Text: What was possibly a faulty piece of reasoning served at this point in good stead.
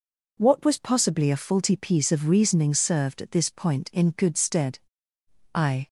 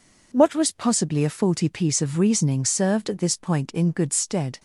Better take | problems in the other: second | goes on to say "I"; slight; from 5.5 s on; 0.32 s long

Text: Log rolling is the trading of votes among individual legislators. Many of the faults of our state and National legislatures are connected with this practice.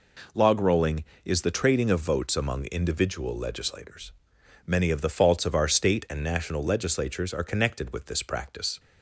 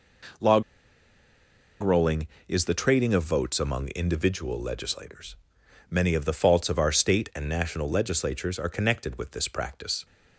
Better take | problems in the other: first | pauses between "Log" and "rolling"; at 0.6 s; 1.1 s long

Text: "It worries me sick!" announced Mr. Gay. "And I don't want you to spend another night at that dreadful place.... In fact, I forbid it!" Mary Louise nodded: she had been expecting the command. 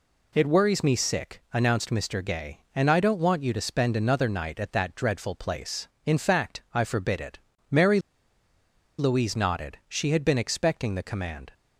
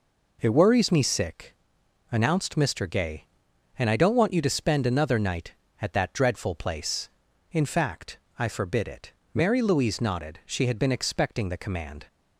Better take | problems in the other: second | pauses between "Mary" and "Louise"; at 7.9 s; 0.98 s long

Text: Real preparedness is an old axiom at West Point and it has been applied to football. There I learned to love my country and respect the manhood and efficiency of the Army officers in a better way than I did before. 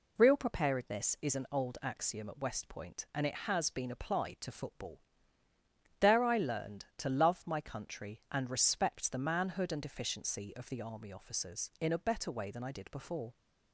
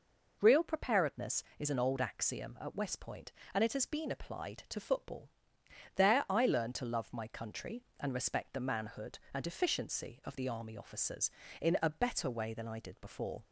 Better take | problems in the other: neither | none

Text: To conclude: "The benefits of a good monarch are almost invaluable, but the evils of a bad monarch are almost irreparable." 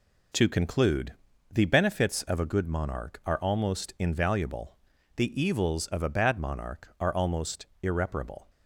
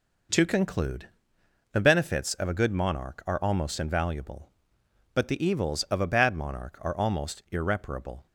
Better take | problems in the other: second | skips "but"; at 4.9 s // pauses between "almost" and "irreparable"; slight; at 7.6 s; 0.16 s long

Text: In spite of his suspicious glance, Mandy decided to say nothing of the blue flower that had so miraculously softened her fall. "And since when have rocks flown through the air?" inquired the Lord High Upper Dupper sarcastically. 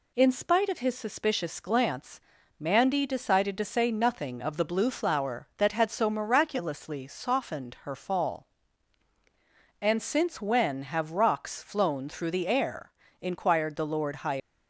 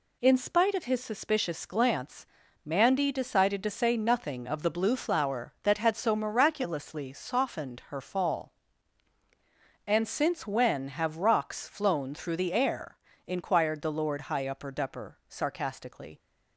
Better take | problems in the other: second | stops before "Upper Dupper sarcastically"; at 14.4 s

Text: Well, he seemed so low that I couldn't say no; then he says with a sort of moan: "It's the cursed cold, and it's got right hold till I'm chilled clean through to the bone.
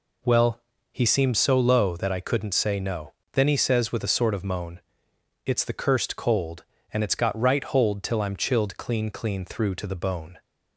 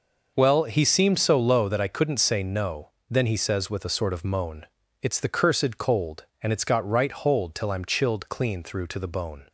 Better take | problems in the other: second | says "clean" twice; at 9.0 s

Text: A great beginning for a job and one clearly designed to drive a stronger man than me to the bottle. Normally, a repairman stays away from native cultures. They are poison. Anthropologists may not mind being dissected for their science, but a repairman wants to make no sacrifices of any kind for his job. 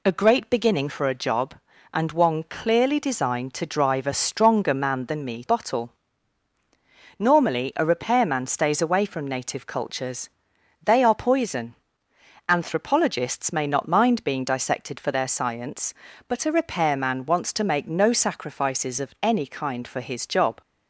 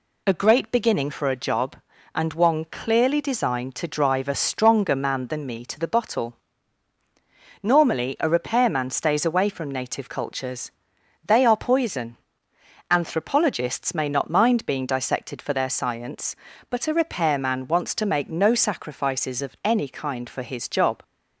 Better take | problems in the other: second | skips "to the"; at 5.4 s

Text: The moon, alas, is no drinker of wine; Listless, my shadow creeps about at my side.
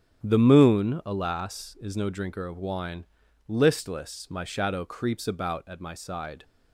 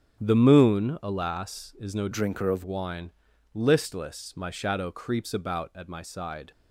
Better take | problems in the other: first | starts louder than the rest; strong; until 1.2 s; 9.5 dB; strong in the first // changes voice from "drinker" to "of"; from 2.1 to 2.6 s; 0.5 s long

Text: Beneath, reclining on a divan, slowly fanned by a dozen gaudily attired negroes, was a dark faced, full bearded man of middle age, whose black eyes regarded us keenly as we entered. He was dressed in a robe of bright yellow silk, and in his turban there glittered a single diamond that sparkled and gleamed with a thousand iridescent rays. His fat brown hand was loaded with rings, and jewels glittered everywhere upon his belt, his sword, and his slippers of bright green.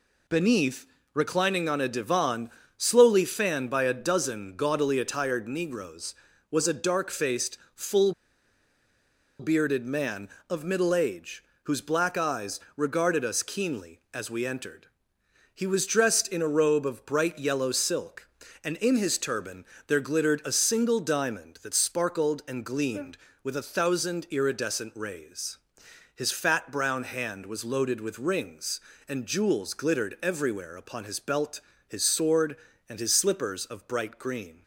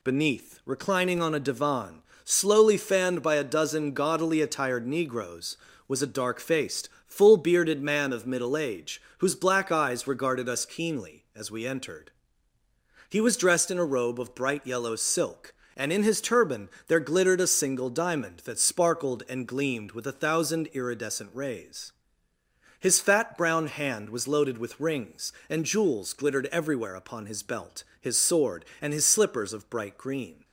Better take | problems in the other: second | pauses between "full" and "bearded"; strong; at 8.1 s; 1.2 s long // pauses between "eyes" and "regarded"; slight; at 12.5 s; 0.16 s long // pauses between "turban" and "there"; slight; at 19.6 s; 0.22 s long; slight in the second

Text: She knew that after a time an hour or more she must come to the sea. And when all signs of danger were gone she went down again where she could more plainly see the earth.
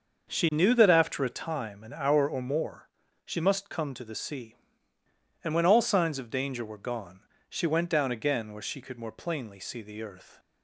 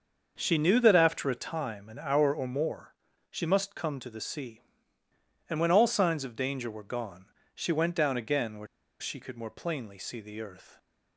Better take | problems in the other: first | starts louder than the rest; until 1.4 s; 6 dB; also in the first // pauses between "more" and "she"; at 2.9 s; 0.38 s long; also in the first // pauses between "gone" and "she"; slight; at 7.2 s; 0.30 s long; slight in the first // pauses between "where" and "she"; slight; at 8.6 s; 0.33 s long

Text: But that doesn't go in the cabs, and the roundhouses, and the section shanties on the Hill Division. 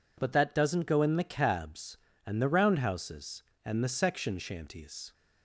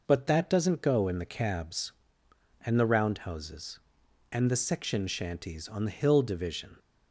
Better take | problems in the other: second | stops before "on the Hill Division"; at 5.1 s

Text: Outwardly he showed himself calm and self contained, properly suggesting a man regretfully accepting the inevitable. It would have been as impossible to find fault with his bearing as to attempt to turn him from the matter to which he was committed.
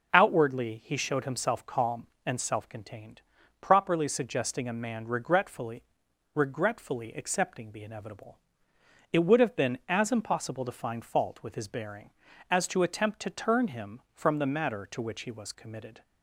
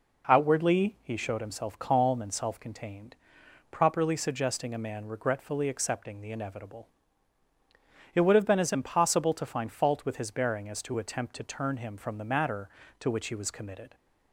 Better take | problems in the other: second | says "regretfully" twice; at 6.3 s

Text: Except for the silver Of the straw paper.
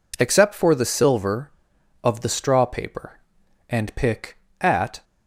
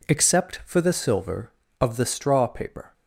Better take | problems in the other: second | goes on to say "And pick At"; from 3.6 s on; 1.3 s long

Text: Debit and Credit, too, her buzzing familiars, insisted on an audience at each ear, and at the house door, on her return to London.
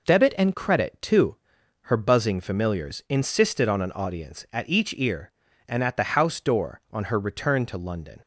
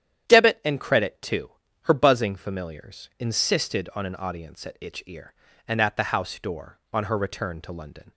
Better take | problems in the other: first | starts louder than the rest; strong; until 1.3 s; 10 dB // says "itch" for "each"; at 4.7 s

